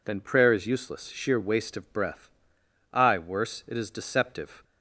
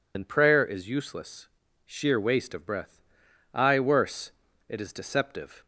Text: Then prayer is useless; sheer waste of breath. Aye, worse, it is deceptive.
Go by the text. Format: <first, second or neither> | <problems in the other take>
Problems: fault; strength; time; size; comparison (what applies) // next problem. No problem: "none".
first | loses the start of "Then"; at 0.1 s; 55 ms